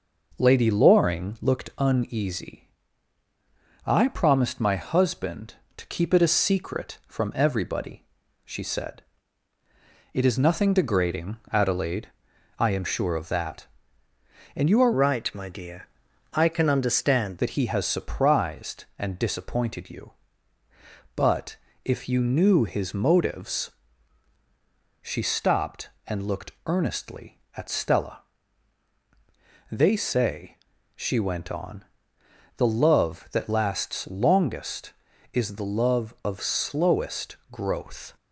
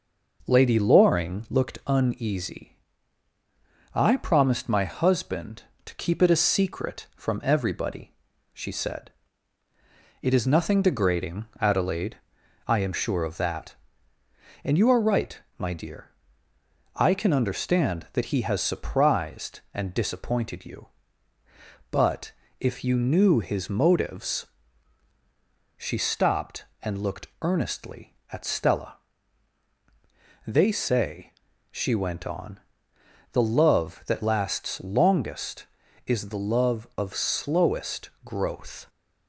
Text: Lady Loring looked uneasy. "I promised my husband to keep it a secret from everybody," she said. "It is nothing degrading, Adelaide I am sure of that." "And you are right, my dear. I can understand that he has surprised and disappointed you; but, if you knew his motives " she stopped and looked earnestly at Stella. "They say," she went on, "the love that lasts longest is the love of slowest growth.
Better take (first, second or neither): second